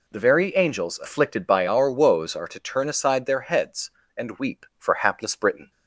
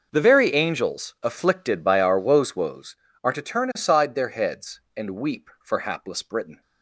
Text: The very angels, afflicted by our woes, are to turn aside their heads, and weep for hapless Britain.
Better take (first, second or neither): first